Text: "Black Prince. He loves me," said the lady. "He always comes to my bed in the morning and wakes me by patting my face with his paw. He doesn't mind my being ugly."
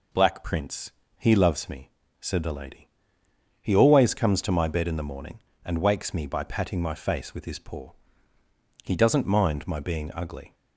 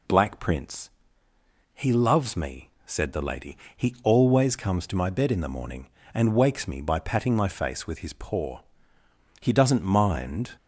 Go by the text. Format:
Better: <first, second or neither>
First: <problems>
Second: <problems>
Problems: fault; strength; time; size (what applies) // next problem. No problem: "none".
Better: first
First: none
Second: stops before "my being ugly"; at 10.5 s